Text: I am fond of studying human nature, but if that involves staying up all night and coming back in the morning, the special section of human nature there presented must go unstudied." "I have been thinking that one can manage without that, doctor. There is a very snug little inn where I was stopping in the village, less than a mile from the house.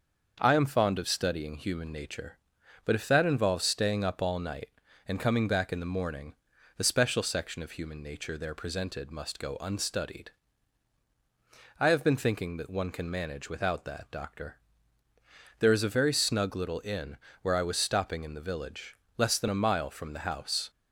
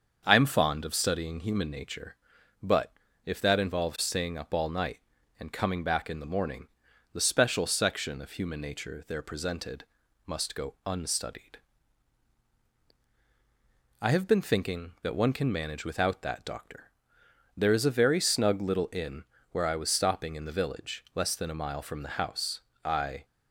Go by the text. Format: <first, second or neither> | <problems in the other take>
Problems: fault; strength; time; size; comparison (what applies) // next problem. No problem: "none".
first | starts louder than the rest; until 1.2 s; 7 dB; also in the first // pauses between "but" and "if"; slight; at 2.9 s; 0.32 s long // pauses between "presented" and "must"; at 9.8 s; 0.40 s long // pauses between "inn" and "where"; slight; at 19.2 s; 0.26 s long; slight in the first // goes on to say "I"; slight; from 22.8 s on; 0.42 s long